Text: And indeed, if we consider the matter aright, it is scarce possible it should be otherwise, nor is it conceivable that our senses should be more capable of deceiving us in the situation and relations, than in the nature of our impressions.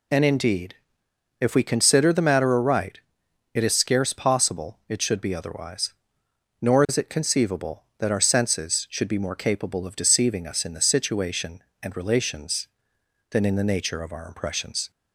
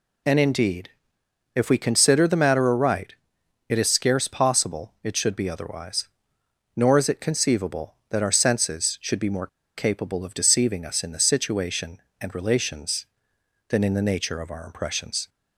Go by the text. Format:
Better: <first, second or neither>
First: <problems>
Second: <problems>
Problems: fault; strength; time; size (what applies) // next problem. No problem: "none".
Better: first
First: none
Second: pauses between "more" and "capable"; slight; at 9.4 s; 0.29 s long